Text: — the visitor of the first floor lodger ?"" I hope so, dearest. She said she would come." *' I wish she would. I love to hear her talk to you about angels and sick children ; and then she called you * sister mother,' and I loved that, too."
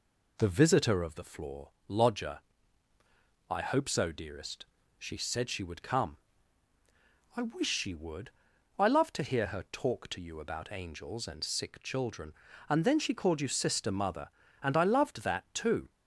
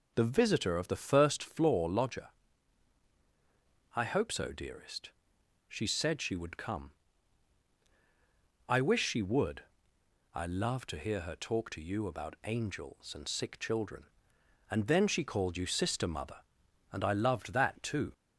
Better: second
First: skips "first"; at 1.2 s // pauses between "floor" and "lodger"; slight; at 1.6 s; 0.18 s long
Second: none

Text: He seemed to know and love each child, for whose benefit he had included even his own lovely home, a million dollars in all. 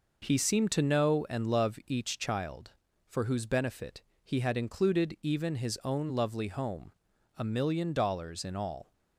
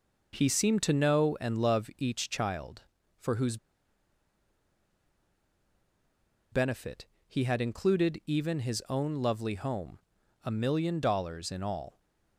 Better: first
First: pauses between "benefit" and "he"; slight; at 4.0 s; 0.20 s long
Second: pauses between "whose" and "benefit"; strong; at 3.5 s; 2.9 s long // pauses between "benefit" and "he"; slight; at 7.0 s; 0.20 s long

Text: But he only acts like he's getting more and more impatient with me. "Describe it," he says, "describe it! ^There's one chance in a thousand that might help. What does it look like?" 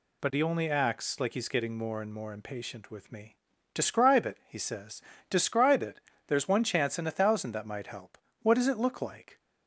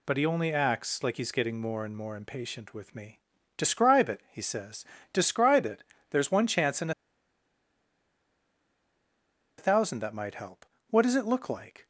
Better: first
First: none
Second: pauses between "in" and "a"; strong; at 6.9 s; 2.6 s long

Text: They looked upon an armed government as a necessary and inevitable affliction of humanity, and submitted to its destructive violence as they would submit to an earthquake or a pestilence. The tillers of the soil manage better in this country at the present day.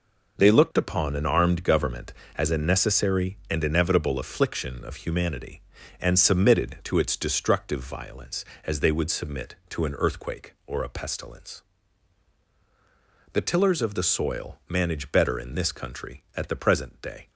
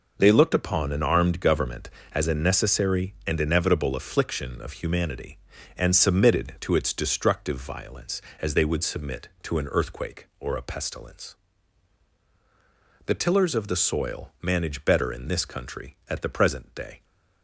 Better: neither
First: none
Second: none

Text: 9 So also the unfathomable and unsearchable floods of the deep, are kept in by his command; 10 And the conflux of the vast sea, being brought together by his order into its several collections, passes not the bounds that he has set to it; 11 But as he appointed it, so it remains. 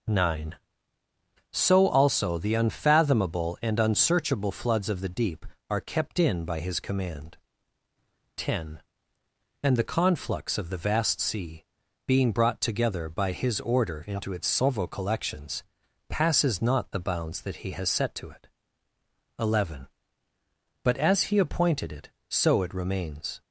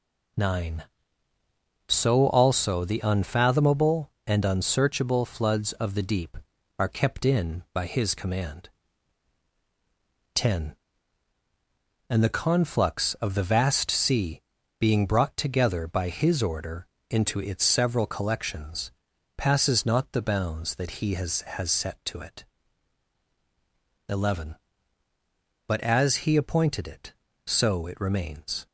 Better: first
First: none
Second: pauses between "order" and "into"; slight; at 16.8 s; 0.22 s long // says "has" twice; at 21.4 s

